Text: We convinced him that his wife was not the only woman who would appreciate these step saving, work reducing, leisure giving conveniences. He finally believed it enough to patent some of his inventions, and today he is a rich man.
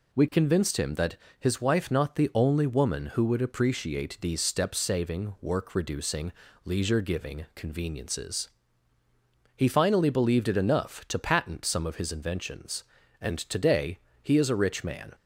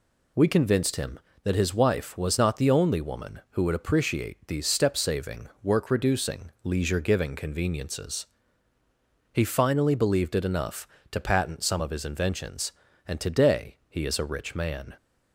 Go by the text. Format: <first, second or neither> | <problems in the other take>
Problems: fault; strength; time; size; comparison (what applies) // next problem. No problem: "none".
second | pauses between "that" and "his"; slight; at 1.1 s; 0.22 s long // skips "was"; at 1.9 s // pauses between "today" and "he"; slight; at 13.9 s; 0.24 s long